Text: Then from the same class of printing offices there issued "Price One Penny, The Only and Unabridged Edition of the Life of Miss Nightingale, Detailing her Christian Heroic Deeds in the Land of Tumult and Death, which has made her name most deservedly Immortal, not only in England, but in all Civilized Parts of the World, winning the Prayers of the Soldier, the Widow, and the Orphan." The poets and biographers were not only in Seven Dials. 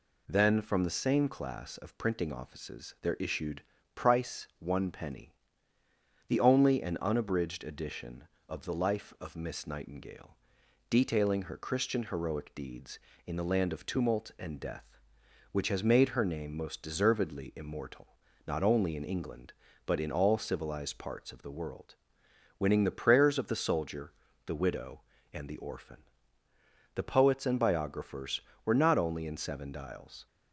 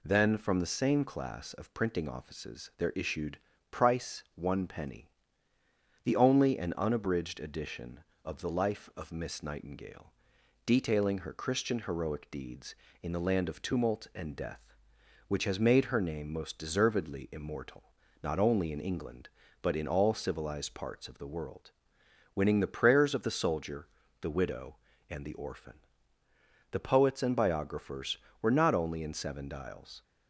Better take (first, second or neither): neither